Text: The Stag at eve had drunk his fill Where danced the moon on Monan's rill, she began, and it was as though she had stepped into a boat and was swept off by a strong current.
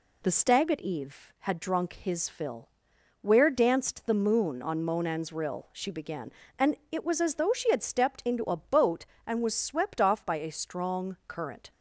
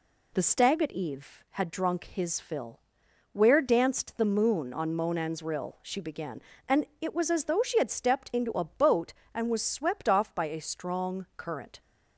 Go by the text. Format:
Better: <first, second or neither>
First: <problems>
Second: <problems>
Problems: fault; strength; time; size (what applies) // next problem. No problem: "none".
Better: neither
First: pauses between "fill" and "Where"; noticeable; at 2.6 s; 0.54 s long // pauses between "and" and "it"; slight; at 6.7 s; 0.16 s long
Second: pauses between "fill" and "Where"; noticeable; at 2.7 s; 0.54 s long // pauses between "and" and "it"; slight; at 6.8 s; 0.16 s long